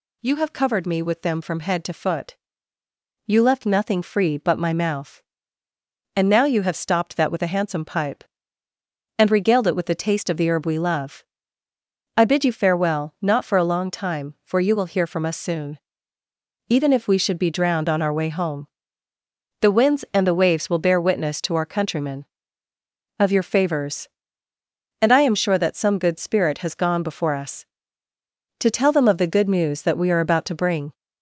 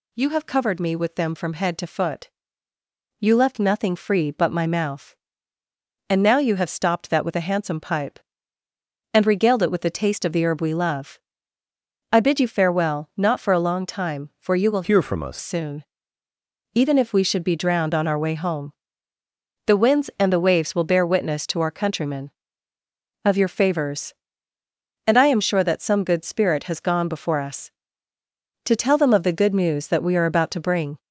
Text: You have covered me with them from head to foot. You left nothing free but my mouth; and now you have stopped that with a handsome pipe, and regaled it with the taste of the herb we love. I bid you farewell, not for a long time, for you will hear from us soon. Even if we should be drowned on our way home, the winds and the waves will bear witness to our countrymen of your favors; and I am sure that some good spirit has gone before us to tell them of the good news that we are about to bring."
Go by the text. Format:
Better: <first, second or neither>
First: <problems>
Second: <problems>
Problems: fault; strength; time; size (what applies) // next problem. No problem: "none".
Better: first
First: none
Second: changes voice from "hear" to "us"; from 14.8 to 15.3 s; 0.5 s long